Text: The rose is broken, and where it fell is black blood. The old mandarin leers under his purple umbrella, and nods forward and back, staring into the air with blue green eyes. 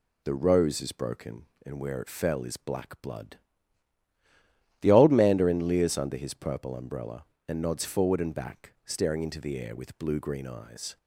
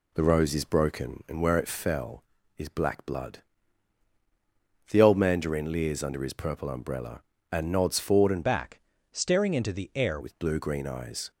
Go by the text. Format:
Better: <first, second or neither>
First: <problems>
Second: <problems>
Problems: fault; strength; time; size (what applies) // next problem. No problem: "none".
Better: first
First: none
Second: changes voice from "back" to "air"; from 8.4 to 10.1 s; 1.7 s long